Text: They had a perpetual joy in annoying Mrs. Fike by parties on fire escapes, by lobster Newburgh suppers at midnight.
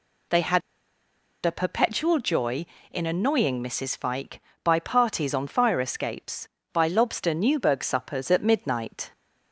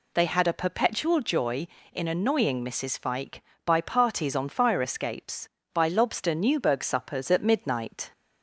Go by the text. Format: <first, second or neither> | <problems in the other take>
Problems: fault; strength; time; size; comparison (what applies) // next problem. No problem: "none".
second | pauses between "had" and "a"; noticeable; at 0.6 s; 0.85 s long